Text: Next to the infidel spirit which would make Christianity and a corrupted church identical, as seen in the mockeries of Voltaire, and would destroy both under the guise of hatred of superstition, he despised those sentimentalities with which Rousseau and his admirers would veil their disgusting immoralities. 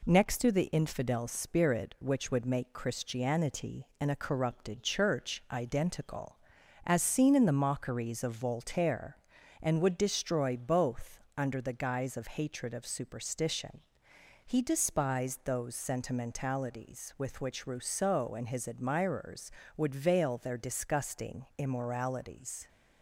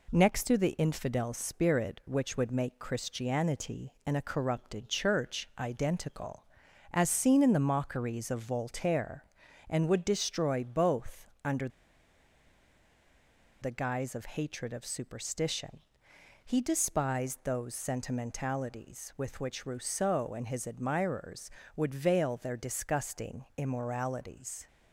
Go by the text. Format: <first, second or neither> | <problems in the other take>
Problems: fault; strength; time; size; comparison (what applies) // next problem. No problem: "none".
first | pauses between "both" and "under"; slight; at 11.2 s; 0.16 s long; slight in the first // pauses between "under" and "the"; strong; at 11.6 s; 1.9 s long